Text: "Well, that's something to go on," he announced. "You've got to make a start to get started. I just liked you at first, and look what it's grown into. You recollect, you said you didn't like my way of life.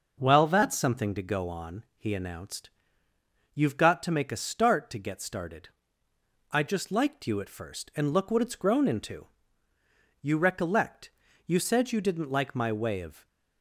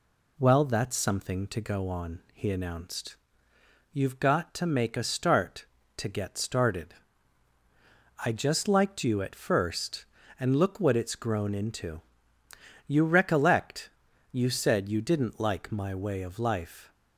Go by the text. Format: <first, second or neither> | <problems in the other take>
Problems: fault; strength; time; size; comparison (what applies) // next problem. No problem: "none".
second | stops before "life"; at 13.2 s